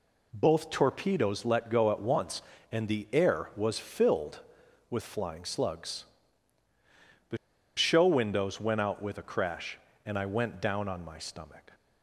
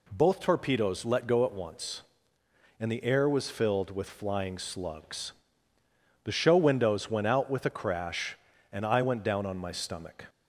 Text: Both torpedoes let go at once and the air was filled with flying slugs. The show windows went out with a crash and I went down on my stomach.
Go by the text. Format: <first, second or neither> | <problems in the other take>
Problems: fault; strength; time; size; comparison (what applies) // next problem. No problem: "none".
second | pauses between "The" and "show"; at 7.3 s; 0.40 s long